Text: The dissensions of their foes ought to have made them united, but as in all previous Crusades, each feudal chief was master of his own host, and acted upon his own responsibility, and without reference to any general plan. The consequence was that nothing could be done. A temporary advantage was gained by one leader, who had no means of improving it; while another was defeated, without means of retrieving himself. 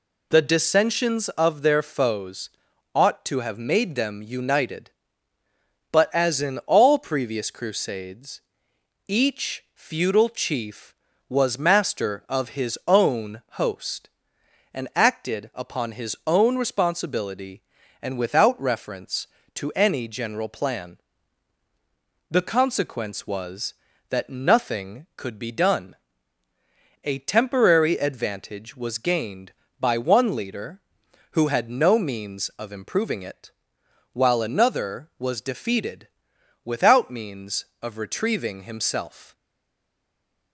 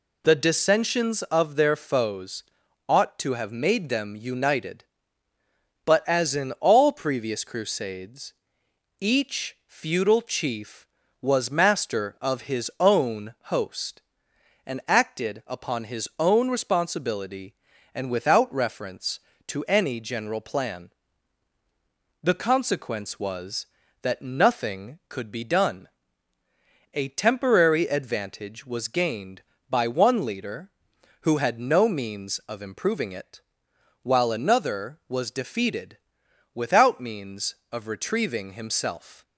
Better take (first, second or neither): second